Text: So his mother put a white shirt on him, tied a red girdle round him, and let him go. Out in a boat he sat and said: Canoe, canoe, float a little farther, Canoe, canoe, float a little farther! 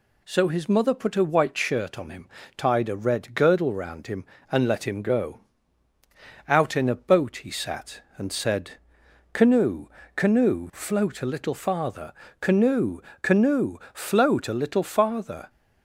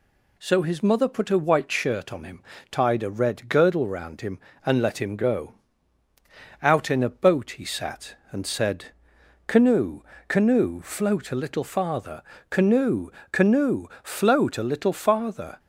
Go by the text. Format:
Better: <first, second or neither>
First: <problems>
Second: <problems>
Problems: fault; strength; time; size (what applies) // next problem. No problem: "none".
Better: neither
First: none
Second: none